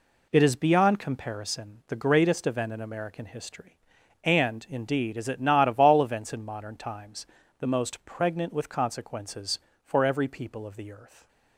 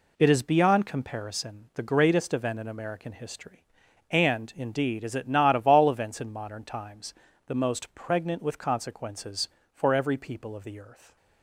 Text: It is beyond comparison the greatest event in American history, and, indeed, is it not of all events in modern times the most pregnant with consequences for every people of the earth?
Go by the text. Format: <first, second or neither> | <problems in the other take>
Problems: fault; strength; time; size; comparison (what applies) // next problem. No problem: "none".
neither | pauses between "times" and "the"; slight; the same in both